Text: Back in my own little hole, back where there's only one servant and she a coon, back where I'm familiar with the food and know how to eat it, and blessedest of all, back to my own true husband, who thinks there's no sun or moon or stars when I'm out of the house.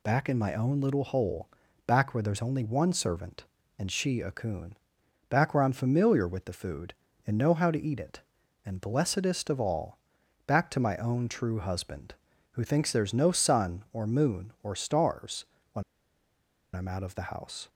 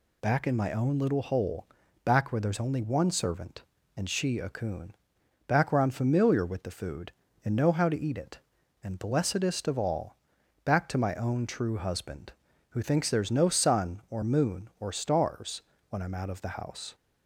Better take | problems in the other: second | pauses between "stars" and "when"; slight; at 15.4 s; 0.26 s long; slight in the second // pauses between "when" and "I'm"; noticeable; at 15.8 s; 0.91 s long

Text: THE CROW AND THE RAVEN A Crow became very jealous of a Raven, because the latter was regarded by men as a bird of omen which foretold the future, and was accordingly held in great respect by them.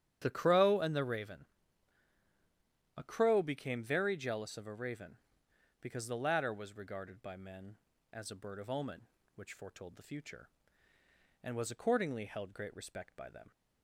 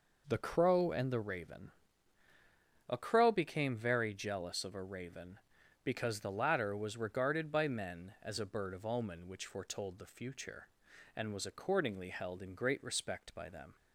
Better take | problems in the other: second | starts louder than the rest; strong; until 1.2 s; 9.5 dB // pauses between "RAVEN" and "A"; strong; at 1.4 s; 1.5 s long; also in the second // skips "in"; at 12.5 s

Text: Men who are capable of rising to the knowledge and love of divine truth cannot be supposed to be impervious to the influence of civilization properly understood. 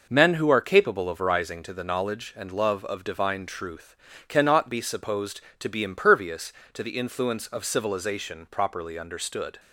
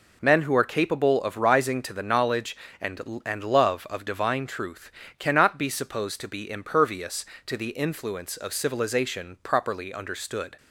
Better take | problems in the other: first | says "and" twice; at 3.2 s // pauses between "truth" and "cannot"; slight; at 4.9 s; 0.26 s long; slight in the first

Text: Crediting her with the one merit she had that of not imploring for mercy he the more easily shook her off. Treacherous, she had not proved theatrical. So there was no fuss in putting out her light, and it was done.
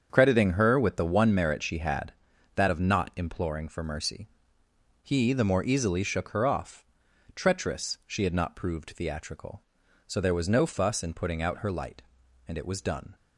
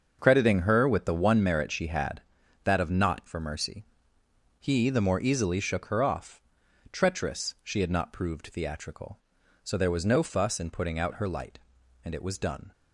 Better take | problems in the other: first | starts louder than the rest; until 1.2 s; 6.5 dB; strong in the first // skips "imploring"; at 3.2 s // pauses between "mercy" and "he"; noticeable; at 3.8 s; 0.76 s long; noticeable in the first

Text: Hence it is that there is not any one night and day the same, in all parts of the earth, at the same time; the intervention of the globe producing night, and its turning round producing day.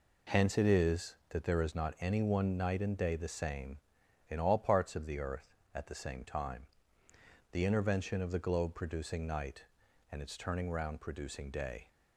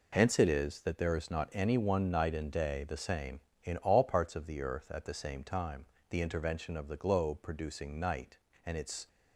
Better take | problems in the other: first | stops before "turning round producing day"; at 9.0 s

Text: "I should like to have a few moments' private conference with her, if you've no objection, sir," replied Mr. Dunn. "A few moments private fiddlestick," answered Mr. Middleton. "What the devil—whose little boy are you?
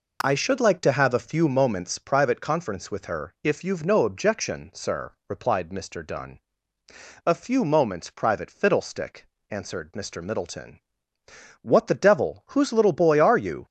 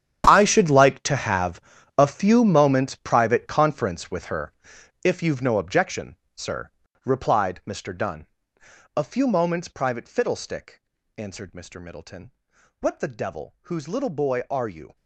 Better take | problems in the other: first | gets quieter; strong; throughout; 14.5 dB // pauses between "have" and "a"; at 1.6 s; 0.38 s long

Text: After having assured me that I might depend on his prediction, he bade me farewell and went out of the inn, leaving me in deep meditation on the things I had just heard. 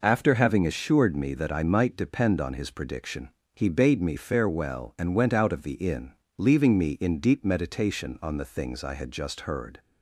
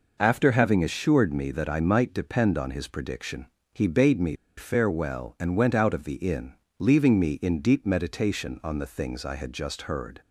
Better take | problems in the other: first | pauses between "me" and "farewell"; slight; at 4.3 s; 0.22 s long

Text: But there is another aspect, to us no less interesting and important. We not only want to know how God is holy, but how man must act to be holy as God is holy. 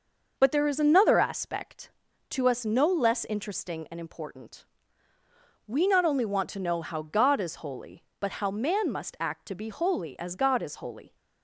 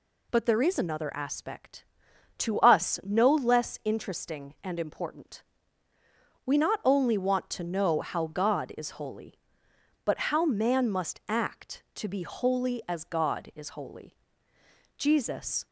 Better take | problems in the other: first | goes on to say "Jesus"; noticeable; from 14.9 s on; 0.70 s long

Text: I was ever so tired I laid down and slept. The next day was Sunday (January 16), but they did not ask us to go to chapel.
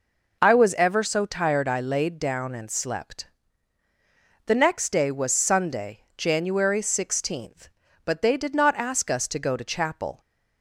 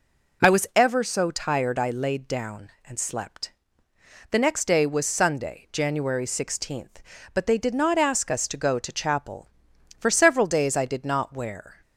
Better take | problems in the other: first | goes on to say "For several days I did not wear"; strong; from 9.9 s on; 1.8 s long

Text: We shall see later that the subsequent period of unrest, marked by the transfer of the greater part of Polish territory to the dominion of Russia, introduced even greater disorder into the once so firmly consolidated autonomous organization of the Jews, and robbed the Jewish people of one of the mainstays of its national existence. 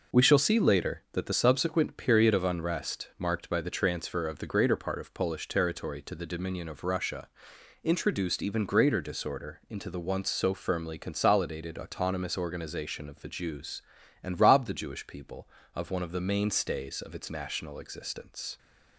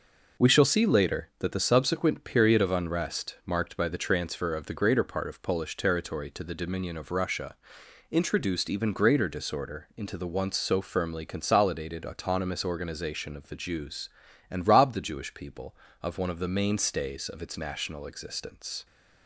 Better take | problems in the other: neither | none

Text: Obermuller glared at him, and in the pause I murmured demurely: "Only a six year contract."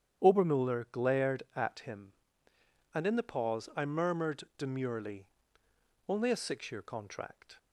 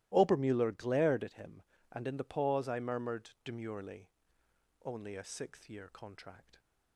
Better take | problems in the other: first | starts louder than the rest; strong; until 1.1 s; 16 dB; strong in the first // says "sixth" for "six"; at 5.2 s

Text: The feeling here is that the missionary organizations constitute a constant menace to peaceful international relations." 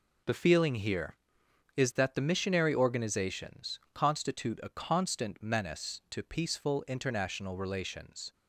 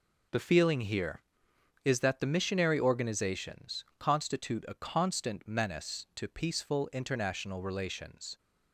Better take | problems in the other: neither | pauses between "organizations" and "constitute"; slight; the same in both

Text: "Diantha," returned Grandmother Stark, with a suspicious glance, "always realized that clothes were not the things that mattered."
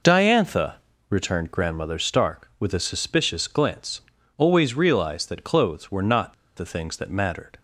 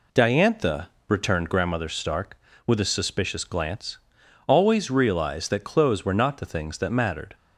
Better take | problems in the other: second | pauses between "not" and "the"; slight; at 6.3 s; 0.23 s long

